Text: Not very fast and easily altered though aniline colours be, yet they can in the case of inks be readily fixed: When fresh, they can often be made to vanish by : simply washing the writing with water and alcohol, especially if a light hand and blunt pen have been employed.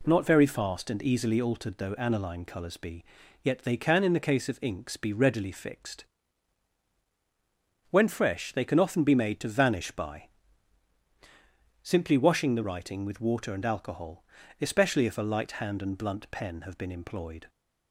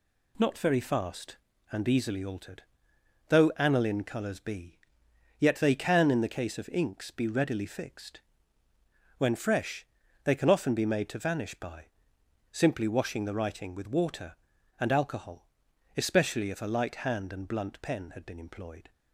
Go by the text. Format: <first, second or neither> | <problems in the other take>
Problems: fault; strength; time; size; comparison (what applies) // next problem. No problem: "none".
first | pauses between "altered" and "though"; noticeable; at 2.6 s; 0.66 s long // says "had" for "have"; at 18.1 s